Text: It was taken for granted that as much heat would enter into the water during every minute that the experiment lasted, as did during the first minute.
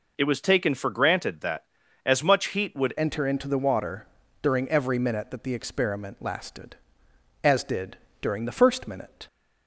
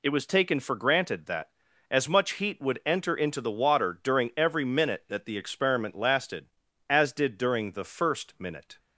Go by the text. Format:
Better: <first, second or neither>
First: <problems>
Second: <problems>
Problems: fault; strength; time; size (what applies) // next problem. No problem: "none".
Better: second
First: changes voice at "enter"; from 2.9 s on; 6.3 s long // pauses between "water" and "during"; at 4.0 s; 0.38 s long // pauses between "did" and "during"; slight; at 7.9 s; 0.24 s long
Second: none